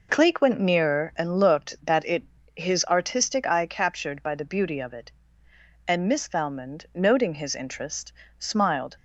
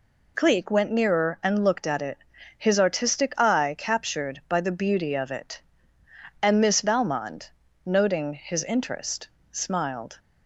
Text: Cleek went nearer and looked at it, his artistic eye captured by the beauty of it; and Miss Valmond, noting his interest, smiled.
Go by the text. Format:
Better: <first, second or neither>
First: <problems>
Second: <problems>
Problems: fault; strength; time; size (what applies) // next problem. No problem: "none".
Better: second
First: says "that" for "at"; at 1.8 s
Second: none